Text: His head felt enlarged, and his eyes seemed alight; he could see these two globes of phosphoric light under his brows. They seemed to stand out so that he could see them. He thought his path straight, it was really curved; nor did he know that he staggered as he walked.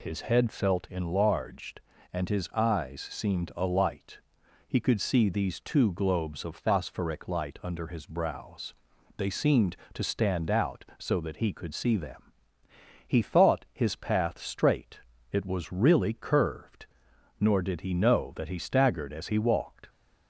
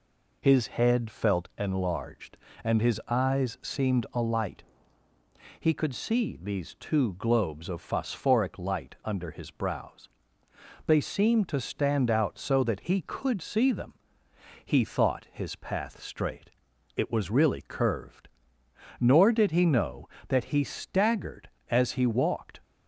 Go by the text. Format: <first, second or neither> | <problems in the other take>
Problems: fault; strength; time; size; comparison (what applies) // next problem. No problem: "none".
neither | none